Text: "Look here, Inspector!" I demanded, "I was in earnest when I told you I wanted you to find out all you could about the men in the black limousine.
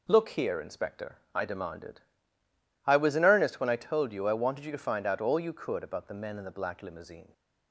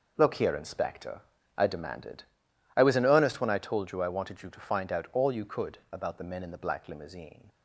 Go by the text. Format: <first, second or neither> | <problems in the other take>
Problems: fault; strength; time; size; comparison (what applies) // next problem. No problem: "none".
neither | none